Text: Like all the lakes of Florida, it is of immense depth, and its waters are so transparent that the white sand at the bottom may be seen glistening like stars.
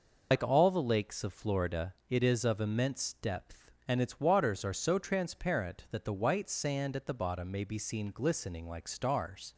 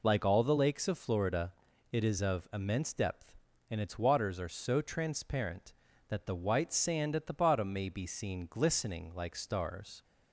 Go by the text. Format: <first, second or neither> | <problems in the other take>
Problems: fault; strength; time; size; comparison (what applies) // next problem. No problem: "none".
second | loses the start of "Like"; at 0.3 s; 95 ms